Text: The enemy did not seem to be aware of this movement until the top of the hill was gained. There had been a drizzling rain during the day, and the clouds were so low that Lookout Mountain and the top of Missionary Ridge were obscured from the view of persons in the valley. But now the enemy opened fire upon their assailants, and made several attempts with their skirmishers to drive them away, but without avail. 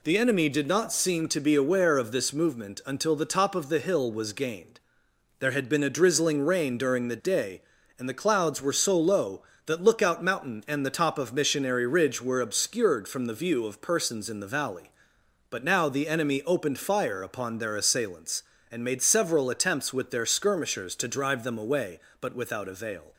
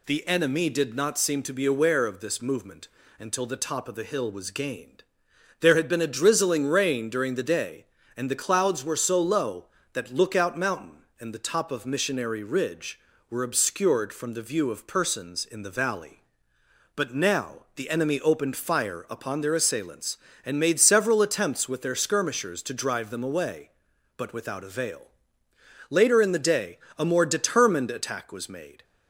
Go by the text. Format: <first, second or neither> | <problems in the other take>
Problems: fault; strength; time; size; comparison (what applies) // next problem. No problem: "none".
first | pauses between "movement" and "until"; slight; at 2.8 s; 0.30 s long // goes on to say "Later in the day a more determined attack was made"; strong; from 25.8 s on; 2.9 s long